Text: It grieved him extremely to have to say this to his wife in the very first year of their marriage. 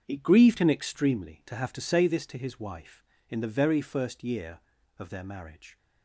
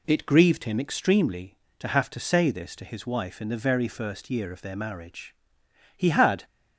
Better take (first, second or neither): first